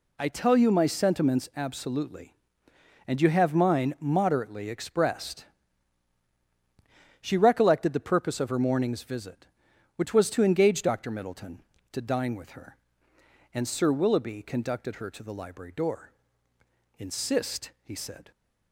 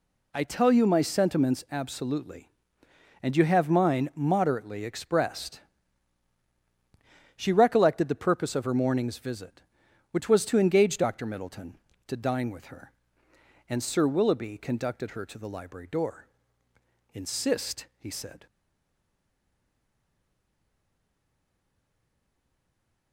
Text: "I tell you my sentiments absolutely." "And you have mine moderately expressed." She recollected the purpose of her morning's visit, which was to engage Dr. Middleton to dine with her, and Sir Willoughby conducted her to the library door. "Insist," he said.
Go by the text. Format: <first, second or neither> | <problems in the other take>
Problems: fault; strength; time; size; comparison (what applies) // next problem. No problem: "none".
first | stays silent after the last word; strong; from 18.4 s on; 4.7 s long